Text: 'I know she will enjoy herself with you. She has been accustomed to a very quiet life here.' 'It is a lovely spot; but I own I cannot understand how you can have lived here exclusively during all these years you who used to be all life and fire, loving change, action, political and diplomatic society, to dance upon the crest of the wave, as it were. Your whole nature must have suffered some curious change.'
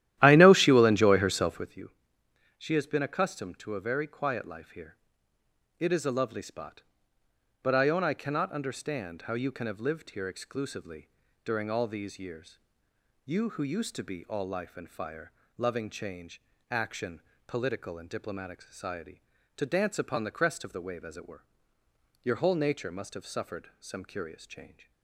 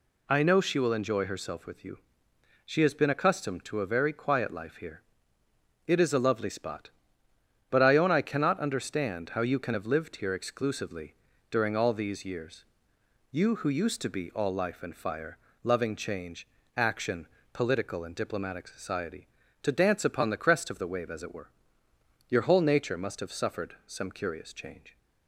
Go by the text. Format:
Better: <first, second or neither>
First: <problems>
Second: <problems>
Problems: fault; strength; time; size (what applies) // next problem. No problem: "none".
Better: second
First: starts louder than the rest; strong; until 1.9 s; 13 dB // pauses between "exclusively" and "during"; slight; at 11.0 s; 0.34 s long // pauses between "years" and "you"; noticeable; at 12.5 s; 0.70 s long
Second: pauses between "exclusively" and "during"; slight; at 11.1 s; 0.34 s long // pauses between "years" and "you"; noticeable; at 12.6 s; 0.70 s long